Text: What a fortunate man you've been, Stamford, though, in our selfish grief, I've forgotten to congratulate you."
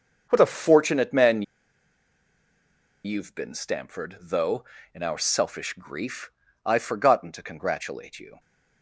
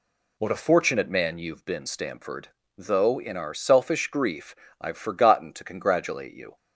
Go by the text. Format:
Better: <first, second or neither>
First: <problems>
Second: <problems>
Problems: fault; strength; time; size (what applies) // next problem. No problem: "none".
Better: second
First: starts louder than the rest; until 1.3 s; 6.5 dB // pauses between "man" and "you've"; strong; at 1.4 s; 1.6 s long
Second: none